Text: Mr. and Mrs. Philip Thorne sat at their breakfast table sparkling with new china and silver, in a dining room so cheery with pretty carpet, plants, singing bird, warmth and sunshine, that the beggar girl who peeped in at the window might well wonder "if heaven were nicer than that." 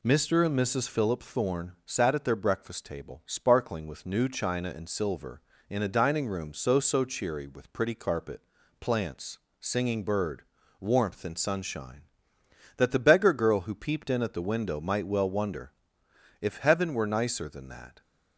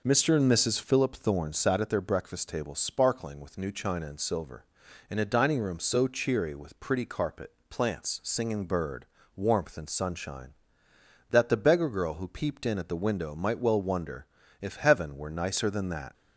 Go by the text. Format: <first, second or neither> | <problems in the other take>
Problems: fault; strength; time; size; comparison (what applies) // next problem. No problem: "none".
second | says "so" twice; at 6.7 s // pauses between "wonder" and "if"; noticeable; at 15.7 s; 0.70 s long; slight in the second